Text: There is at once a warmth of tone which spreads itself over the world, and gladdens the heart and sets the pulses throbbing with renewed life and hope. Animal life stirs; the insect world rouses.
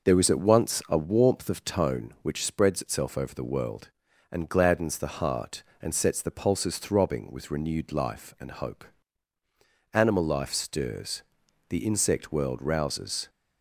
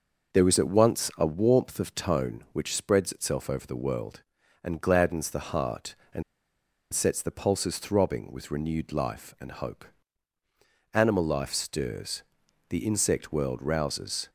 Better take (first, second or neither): first